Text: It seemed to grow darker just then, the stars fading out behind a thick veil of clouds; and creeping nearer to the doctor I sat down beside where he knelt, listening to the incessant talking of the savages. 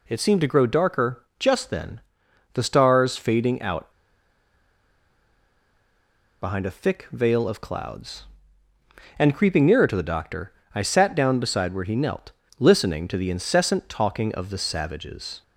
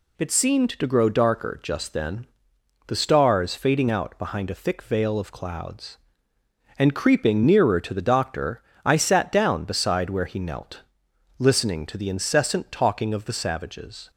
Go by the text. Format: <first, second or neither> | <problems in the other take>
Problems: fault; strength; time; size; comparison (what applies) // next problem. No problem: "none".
second | pauses between "out" and "behind"; strong; at 3.9 s; 2.4 s long // pauses between "doctor" and "I"; slight; at 10.5 s; 0.22 s long; slight in the second